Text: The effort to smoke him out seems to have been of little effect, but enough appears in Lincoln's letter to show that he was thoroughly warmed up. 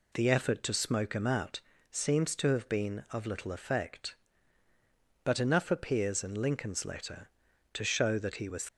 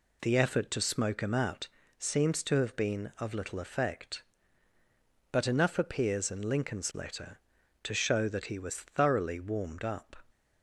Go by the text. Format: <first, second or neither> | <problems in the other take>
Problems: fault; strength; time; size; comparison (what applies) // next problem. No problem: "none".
second | pauses between "out" and "seems"; slight; at 1.5 s; 0.30 s long; slight in the second // stops before "thoroughly warmed up"; at 8.6 s